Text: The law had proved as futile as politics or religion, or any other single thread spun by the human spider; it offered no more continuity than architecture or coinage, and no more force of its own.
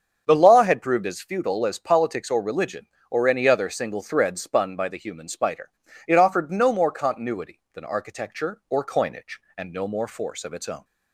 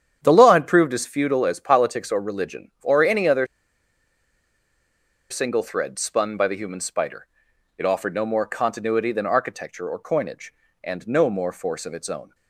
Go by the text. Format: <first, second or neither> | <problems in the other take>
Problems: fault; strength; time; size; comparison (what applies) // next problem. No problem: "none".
first | starts louder than the rest; strong; until 1.2 s; 9 dB; also in the first // pauses between "other" and "single"; strong; at 3.4 s; 1.8 s long